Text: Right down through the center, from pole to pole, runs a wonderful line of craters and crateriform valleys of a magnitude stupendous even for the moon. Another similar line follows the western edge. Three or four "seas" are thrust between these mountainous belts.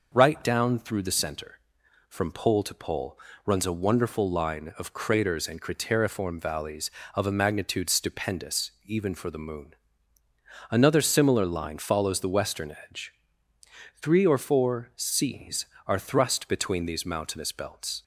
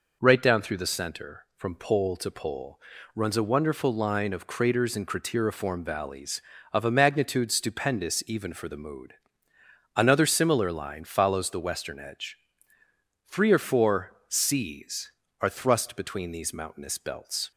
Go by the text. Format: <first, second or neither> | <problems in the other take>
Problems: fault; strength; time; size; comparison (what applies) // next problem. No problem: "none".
first | says "mood" for "moon"; at 8.7 s